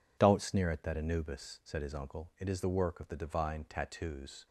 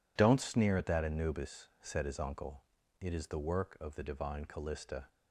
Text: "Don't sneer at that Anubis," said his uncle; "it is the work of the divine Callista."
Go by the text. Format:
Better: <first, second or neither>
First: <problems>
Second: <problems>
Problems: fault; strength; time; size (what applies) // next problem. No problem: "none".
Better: second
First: says "Tattoos" for "Callista"; at 3.6 s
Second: none